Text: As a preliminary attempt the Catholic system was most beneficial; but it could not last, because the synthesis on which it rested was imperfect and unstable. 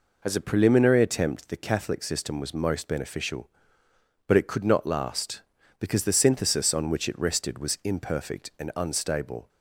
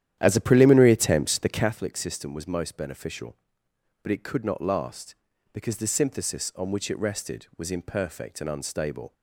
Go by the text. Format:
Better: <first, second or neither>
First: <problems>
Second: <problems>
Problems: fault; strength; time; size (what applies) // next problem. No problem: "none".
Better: first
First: none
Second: starts louder than the rest; strong; until 1.7 s; 11 dB